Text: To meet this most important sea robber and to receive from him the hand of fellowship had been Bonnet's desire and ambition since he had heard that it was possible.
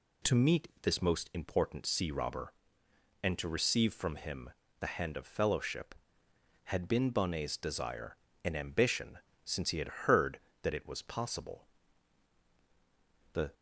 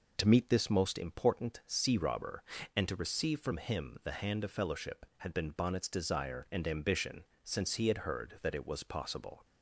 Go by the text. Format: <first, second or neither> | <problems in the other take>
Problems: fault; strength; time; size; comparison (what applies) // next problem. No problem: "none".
second | pauses between "him" and "the"; slight; at 4.5 s; 0.28 s long // pauses between "ambition" and "since"; slight; at 9.1 s; 0.24 s long; slight in the second // goes on to say "The"; slight; from 13.3 s on; 0.20 s long